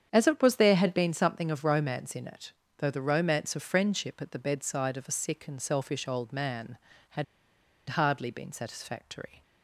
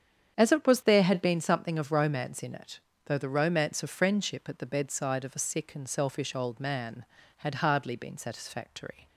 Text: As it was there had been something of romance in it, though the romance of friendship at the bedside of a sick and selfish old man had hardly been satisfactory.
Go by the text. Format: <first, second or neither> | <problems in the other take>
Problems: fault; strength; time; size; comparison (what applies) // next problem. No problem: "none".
second | starts louder than the rest; strong; until 1.1 s; 8.5 dB; strong in the second // pauses between "had" and "hardly"; noticeable; at 7.2 s; 0.64 s long